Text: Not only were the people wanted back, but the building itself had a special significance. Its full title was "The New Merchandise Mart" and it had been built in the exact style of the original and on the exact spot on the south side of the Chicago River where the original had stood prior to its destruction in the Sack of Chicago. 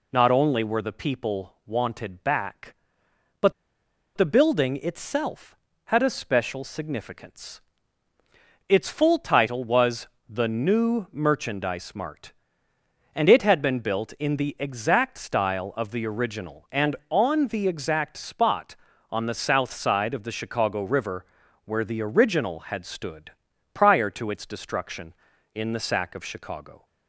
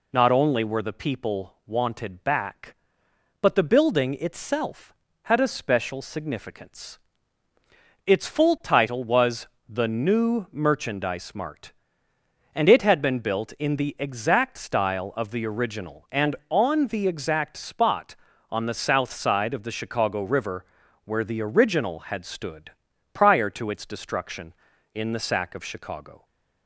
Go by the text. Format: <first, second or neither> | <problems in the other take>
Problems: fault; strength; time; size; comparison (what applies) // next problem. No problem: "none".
second | pauses between "but" and "the"; noticeable; at 3.5 s; 0.64 s long // pauses between "was" and "The"; slight; at 10.0 s; 0.20 s long; slight in the second // pauses between "River" and "where"; at 21.2 s; 0.40 s long; also in the second // pauses between "stood" and "prior"; at 23.3 s; 0.42 s long; also in the second